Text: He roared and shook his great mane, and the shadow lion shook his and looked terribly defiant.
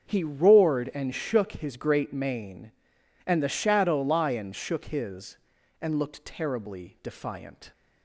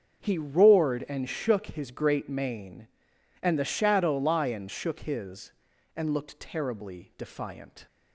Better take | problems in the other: neither | starts louder than the rest; the same in both

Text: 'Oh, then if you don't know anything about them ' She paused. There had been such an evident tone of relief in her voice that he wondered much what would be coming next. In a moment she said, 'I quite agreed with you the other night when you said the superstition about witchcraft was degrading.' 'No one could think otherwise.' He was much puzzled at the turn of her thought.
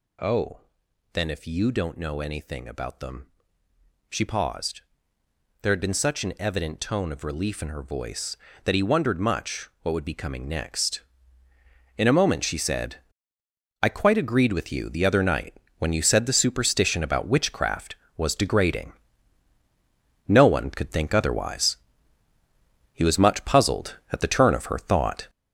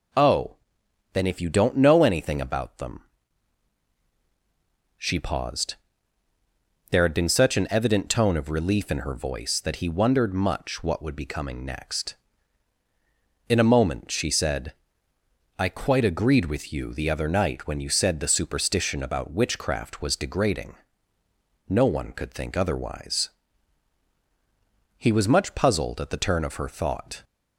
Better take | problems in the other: second | gets louder; strong; throughout; 10 dB // pauses between "night" and "when"; slight; at 15.5 s; 0.22 s long

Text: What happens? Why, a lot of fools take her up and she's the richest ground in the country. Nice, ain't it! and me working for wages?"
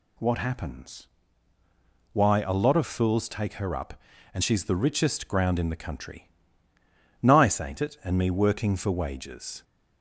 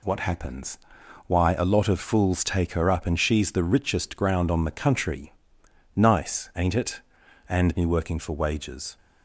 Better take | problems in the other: first | says "on" for "in"; at 4.5 s

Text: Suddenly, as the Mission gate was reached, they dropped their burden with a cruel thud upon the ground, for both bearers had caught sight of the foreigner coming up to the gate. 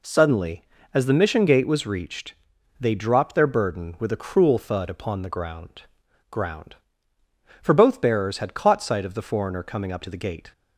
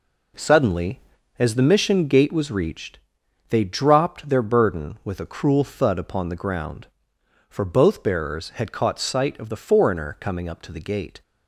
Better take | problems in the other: second | says "ground" twice; at 6.2 s

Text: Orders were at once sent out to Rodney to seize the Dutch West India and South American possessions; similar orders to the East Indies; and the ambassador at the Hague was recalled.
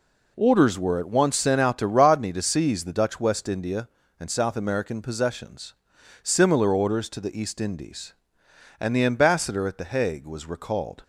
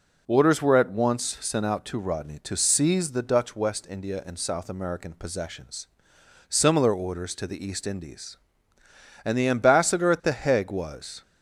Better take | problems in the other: first | stops before "recalled"; at 11.2 s

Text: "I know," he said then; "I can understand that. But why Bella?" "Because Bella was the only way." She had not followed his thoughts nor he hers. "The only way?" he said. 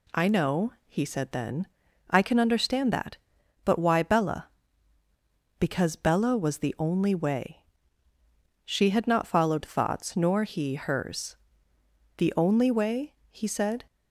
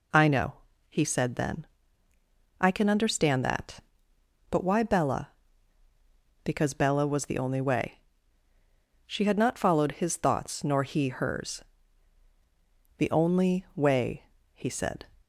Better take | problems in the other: second | skips "his"; at 9.6 s

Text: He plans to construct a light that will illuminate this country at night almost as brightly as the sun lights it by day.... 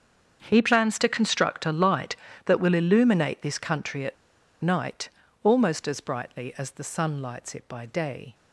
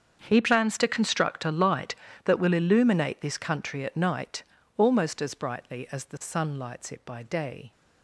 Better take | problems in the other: second | starts louder than the rest; strong; until 1.4 s; 7.5 dB; strong in the second // pauses between "at" and "night"; noticeable; at 4.1 s; 0.46 s long // pauses between "night" and "almost"; slight; at 5.0 s; 0.34 s long; slight in the second

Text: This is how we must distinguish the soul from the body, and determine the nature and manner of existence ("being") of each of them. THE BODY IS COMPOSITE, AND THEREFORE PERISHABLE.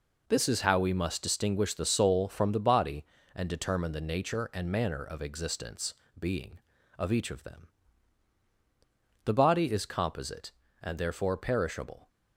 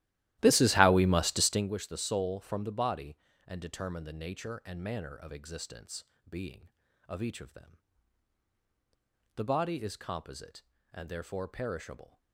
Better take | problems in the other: first | starts louder than the rest; strong; until 1.7 s; 15 dB

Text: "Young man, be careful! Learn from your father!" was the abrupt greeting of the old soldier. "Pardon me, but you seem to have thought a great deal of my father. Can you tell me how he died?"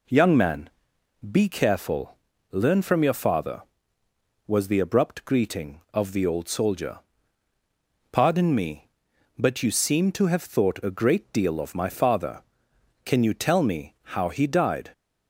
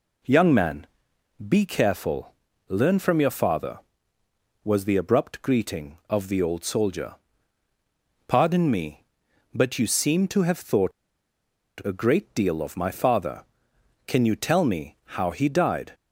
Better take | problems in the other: first | pauses between "thought" and "a"; noticeable; at 10.9 s; 0.90 s long // pauses between "me" and "how"; slight; at 14.9 s; 0.18 s long; slight in the first

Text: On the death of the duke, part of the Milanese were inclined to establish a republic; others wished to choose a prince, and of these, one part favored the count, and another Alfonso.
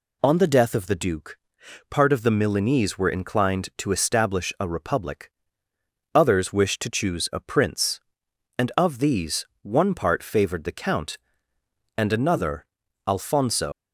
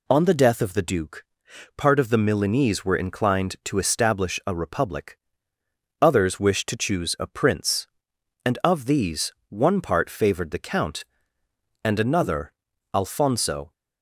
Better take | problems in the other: second | pauses between "another" and "Alfonso"; at 12.6 s; 0.42 s long; also in the second // leaves "Alfonso" unfinished; at 13.7 s; 130 ms

